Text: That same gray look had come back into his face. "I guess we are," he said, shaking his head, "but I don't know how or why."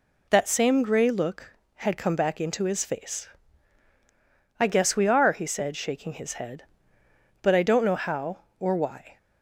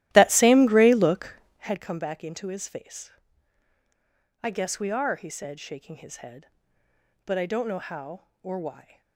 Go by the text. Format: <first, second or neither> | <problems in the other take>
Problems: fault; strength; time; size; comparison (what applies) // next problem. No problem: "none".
first | starts louder than the rest; strong; until 1.8 s; 14.5 dB